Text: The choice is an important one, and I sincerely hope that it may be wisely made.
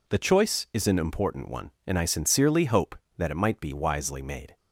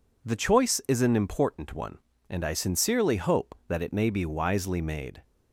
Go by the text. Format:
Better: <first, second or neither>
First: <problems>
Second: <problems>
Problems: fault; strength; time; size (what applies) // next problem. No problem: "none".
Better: second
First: says "might" for "may"; at 3.3 s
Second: none